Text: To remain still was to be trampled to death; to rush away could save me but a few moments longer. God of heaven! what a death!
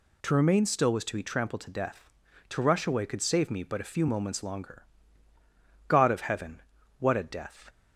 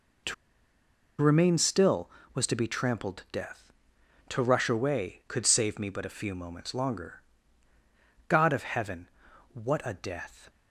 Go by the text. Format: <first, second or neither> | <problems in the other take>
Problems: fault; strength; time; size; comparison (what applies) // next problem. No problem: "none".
first | pauses between "To" and "remain"; noticeable; at 0.3 s; 0.87 s long